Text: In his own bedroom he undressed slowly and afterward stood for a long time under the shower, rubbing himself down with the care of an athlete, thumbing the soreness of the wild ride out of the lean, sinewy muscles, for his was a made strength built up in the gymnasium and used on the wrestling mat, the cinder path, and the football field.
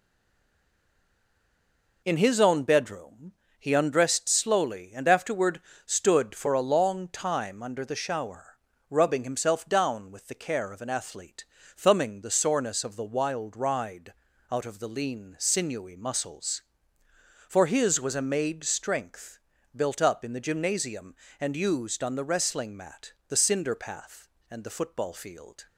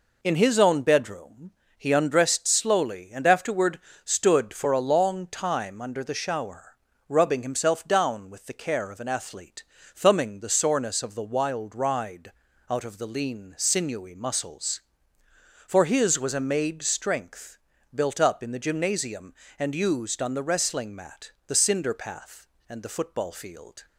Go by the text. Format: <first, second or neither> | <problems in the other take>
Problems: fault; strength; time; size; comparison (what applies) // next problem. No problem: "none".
second | stays silent before the first word; noticeable; until 2.0 s; 2.0 s long // pauses between "bedroom" and "he"; slight; at 3.3 s; 0.26 s long; slight in the second // pauses between "afterward" and "stood"; slight; at 5.6 s; 0.26 s long; slight in the second // pauses between "ride" and "out"; at 14.1 s; 0.38 s long; also in the second // pauses between "strength" and "built"; slight; at 19.3 s; 0.36 s long; slight in the second